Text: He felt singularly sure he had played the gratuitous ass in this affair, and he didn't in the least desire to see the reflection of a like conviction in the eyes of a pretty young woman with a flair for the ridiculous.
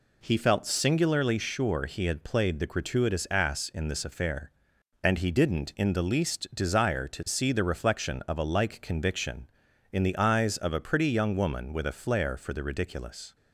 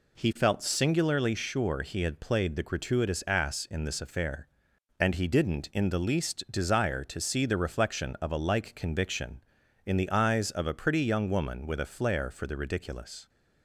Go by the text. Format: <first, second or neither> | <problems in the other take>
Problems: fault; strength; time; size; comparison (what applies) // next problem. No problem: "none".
neither | none